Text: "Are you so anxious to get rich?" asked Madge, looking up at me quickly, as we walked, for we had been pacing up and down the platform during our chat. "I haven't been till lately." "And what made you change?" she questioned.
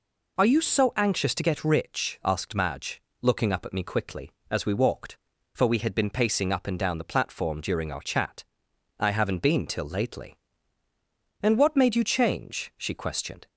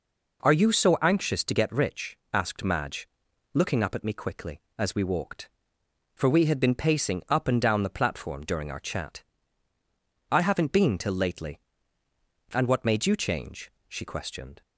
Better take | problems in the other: neither | none

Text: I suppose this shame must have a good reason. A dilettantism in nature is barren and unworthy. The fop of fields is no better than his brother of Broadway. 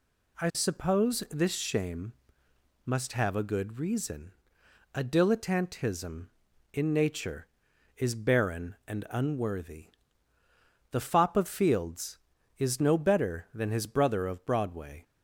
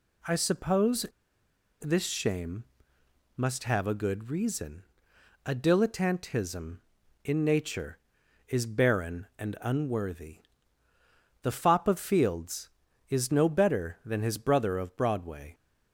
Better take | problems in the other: first | pauses between "suppose" and "this"; noticeable; at 1.0 s; 0.78 s long // pauses between "shame" and "must"; noticeable; at 2.6 s; 0.72 s long; noticeable in the first

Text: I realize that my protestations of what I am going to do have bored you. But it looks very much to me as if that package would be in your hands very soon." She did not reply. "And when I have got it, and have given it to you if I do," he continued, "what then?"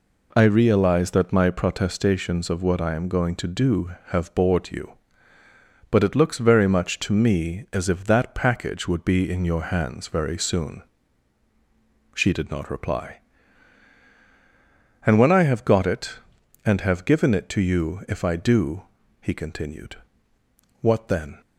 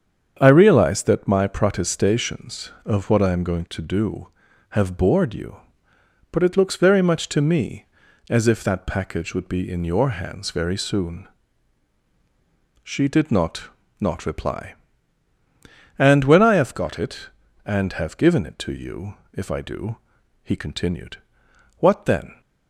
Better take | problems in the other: first | starts louder than the rest; strong; until 1.4 s; 7.5 dB // says "not" twice; at 14.0 s // pauses between "you" and "if"; slight; at 19.1 s; 0.20 s long

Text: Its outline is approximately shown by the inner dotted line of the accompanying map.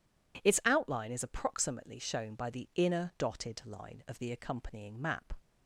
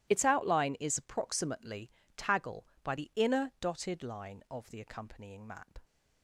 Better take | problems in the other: first | starts louder than the rest; strong; until 1.1 s; 15.5 dB // says "taggle" for "shown"; at 2.1 s

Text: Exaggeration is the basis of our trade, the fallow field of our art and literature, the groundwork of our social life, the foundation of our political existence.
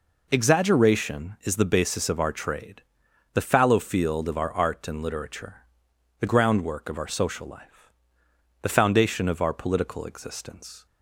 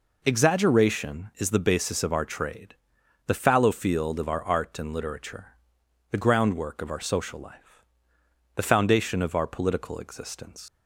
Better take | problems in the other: first | leaves "existence" unfinished; at 10.6 s; 110 ms

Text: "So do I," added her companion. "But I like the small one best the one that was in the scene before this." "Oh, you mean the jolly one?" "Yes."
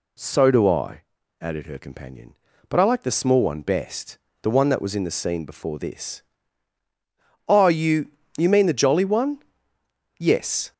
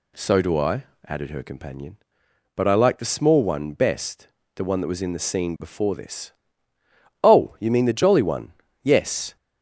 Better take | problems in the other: second | pauses between "best" and "the"; slight; at 4.1 s; 0.24 s long; slight in the second // says "you" twice; at 8.3 s

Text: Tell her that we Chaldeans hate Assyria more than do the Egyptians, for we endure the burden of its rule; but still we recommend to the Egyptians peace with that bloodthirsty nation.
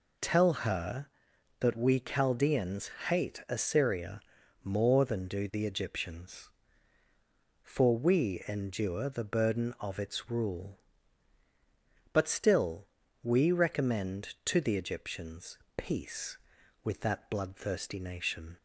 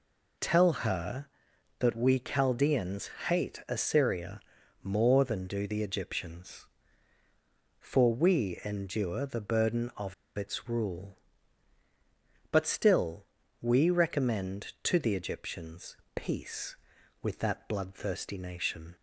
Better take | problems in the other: first | pauses between "Chaldeans" and "hate"; slight; at 3.0 s; 0.18 s long; slight in the first // pauses between "Assyria" and "more"; at 4.3 s; 0.44 s long; also in the first // pauses between "of" and "its"; slight; at 10.1 s; 0.23 s long // pauses between "still" and "we"; slight; at 13.2 s; 0.36 s long; slight in the first // pauses between "Egyptians" and "peace"; slight; at 15.9 s; 0.20 s long; slight in the first

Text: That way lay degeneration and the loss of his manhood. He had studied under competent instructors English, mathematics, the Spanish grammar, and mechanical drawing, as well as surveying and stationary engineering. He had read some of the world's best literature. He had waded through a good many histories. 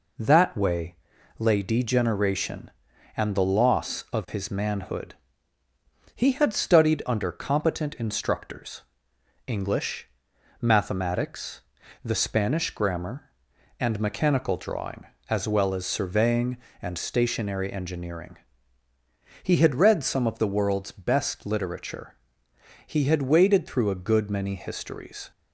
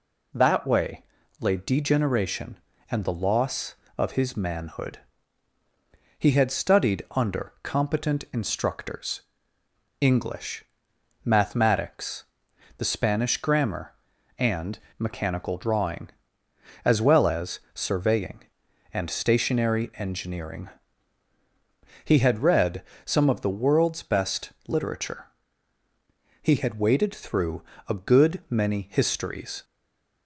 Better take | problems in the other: first | pauses between "way" and "lay"; at 1.0 s; 0.38 s long; also in the first // pauses between "instructors" and "English"; noticeable; at 9.2 s; 0.78 s long; noticeable in the first // pauses between "and" and "mechanical"; slight; at 14.7 s; 0.18 s long // pauses between "read" and "some"; slight; at 22.8 s; 0.22 s long // pauses between "through" and "a"; slight; at 27.6 s; 0.26 s long // stays silent after the last word; slight; from 29.6 s on; 0.6 s long

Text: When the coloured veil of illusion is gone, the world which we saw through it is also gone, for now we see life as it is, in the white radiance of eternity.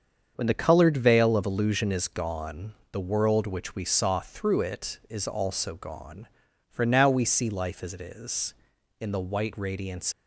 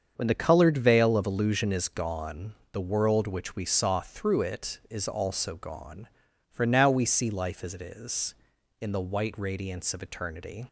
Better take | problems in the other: second | starts louder than the rest; until 1.4 s; 7 dB; also in the second // stops before "of eternity"; at 10.1 s

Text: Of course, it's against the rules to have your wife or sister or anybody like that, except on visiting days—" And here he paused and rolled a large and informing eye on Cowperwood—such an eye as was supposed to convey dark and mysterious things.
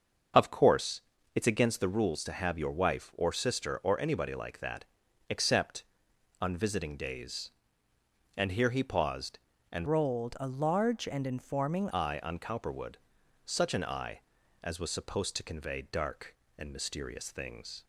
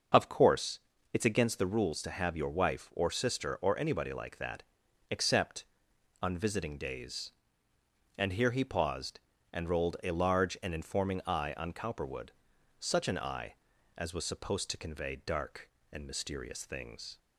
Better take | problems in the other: second | starts louder than the rest; until 1.6 s; 6.5 dB; also in the second // changes voice from "rolled" to "informing"; from 9.8 to 11.8 s; 2.0 s long

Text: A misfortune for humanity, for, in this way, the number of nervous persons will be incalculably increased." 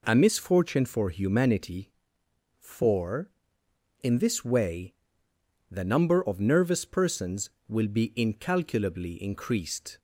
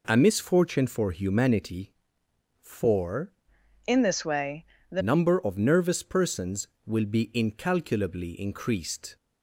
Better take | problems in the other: first | changes voice from "in" to "the"; from 3.8 to 5.0 s; 1.2 s long

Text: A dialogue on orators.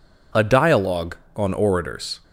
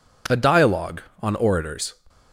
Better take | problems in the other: neither | none

